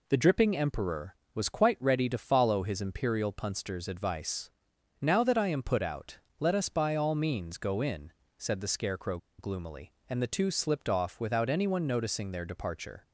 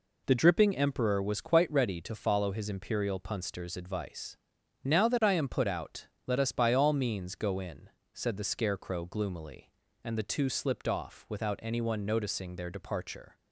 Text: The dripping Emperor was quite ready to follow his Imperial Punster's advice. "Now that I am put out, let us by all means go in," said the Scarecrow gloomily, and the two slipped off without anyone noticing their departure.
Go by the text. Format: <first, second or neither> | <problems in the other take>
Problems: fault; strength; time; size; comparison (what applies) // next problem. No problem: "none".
second | pauses between "Scarecrow" and "gloomily"; slight; at 9.1 s; 0.20 s long